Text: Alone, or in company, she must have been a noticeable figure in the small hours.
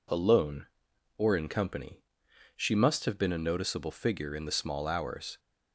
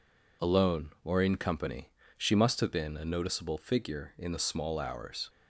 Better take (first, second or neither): neither